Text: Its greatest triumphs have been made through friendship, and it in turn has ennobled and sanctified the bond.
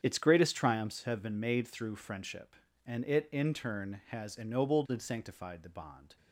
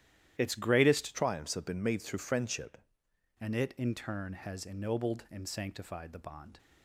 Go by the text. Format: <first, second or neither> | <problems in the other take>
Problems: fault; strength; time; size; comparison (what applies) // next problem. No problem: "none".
first | starts louder than the rest; strong; until 1.3 s; 12 dB; strong in the first // changes voice from "triumphs" to "friendship"; from 1.1 to 2.7 s; 1.6 s long